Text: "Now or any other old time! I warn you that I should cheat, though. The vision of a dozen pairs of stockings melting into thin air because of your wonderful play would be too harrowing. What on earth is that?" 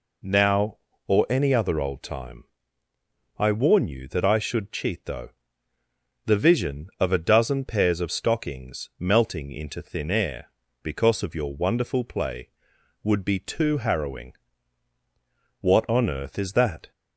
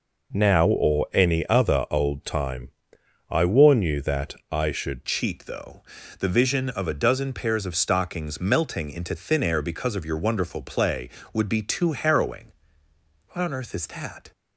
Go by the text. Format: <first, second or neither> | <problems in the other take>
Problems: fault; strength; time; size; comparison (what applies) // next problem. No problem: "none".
first | pauses between "that" and "I"; slight; at 4.3 s; 0.16 s long // changes voice at "cheat"; from 5.0 s on; 9.3 s long